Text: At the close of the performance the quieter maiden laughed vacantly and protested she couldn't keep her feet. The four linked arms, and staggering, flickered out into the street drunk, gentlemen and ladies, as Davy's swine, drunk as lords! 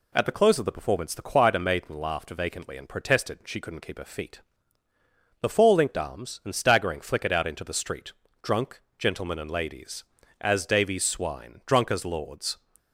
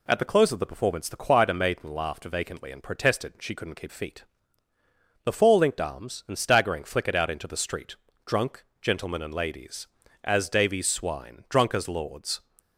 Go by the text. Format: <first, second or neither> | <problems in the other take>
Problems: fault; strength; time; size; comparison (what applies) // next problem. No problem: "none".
first | skips "her"; at 3.8 s // pauses between "street" and "drunk"; slight; at 7.9 s; 0.30 s long; slight in the first